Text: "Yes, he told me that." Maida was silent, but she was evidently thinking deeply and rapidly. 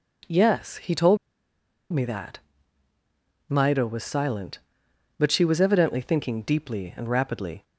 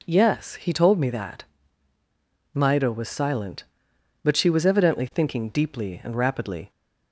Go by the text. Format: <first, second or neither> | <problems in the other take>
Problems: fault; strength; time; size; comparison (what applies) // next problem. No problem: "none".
second | pauses between "told" and "me"; noticeable; at 1.1 s; 0.75 s long